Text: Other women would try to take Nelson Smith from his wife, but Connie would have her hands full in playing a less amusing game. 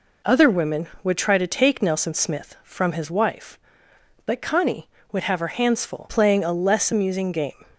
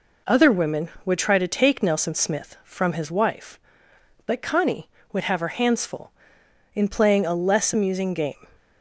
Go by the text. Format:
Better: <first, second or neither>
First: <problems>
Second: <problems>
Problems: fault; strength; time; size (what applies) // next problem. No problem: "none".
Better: second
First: skips "in"; at 6.0 s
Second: none